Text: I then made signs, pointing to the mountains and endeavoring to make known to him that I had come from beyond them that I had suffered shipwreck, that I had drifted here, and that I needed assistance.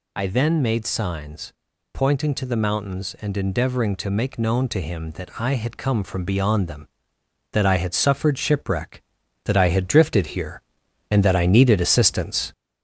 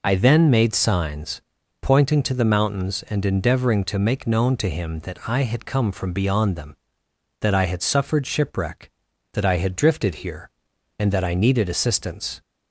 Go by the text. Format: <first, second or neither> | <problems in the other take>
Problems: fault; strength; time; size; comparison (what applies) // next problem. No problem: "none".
second | gets louder; throughout; 3.5 dB